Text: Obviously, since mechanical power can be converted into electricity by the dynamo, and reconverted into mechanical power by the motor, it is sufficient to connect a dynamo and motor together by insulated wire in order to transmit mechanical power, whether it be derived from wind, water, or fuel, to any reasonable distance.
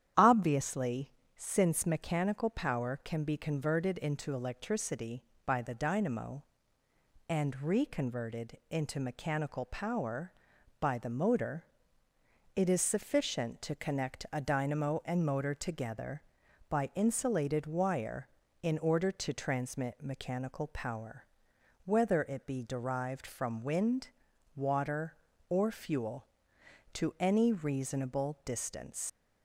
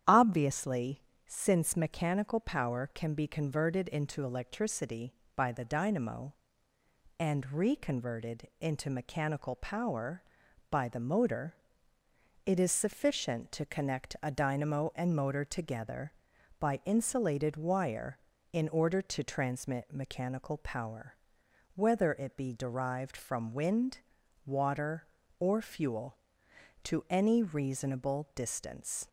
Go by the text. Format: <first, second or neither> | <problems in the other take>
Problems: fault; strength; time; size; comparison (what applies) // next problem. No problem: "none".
second | starts louder than the rest; strong; until 1.4 s; 10 dB; strong in the second // leaves "distance" unfinished; at 29.0 s; 80 ms